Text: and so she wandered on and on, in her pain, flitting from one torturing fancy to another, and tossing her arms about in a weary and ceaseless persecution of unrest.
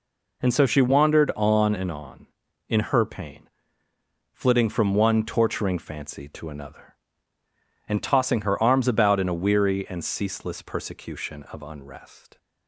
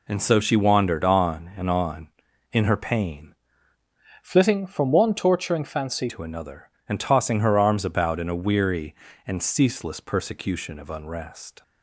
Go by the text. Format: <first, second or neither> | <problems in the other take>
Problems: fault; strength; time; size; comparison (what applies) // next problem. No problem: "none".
first | changes voice from "flitting" to "fancy"; from 4.2 to 6.0 s; 1.8 s long